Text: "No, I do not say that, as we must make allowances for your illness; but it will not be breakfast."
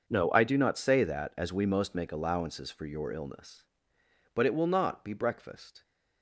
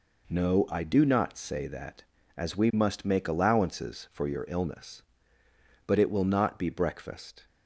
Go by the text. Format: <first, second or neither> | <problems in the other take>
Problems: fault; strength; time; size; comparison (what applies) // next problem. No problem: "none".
second | starts louder than the rest; noticeable; until 1.1 s; 6 dB // says "most" for "must"; at 1.6 s